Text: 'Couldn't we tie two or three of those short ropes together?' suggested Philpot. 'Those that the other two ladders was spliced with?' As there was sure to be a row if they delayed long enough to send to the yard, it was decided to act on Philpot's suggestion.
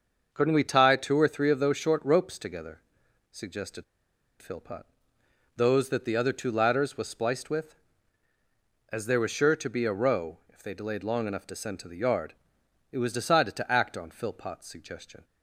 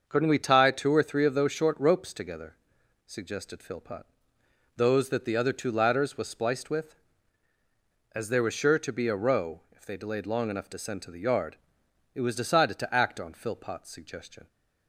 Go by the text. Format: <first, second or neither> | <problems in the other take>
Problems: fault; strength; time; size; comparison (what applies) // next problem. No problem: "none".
second | starts louder than the rest; until 1.3 s; 6.5 dB; also in the second // pauses between "suggested" and "Philpot"; noticeable; at 3.8 s; 0.57 s long